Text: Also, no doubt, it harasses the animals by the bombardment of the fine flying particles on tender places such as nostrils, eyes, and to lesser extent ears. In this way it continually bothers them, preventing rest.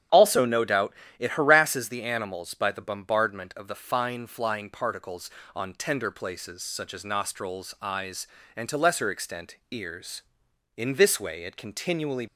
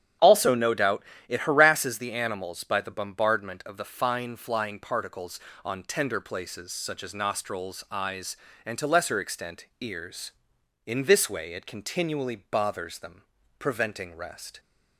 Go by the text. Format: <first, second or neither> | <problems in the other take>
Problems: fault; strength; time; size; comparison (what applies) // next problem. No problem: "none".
second | starts louder than the rest; strong; until 1.3 s; 9.5 dB; strong in the second // stops before "bothers them preventing rest"; at 12.2 s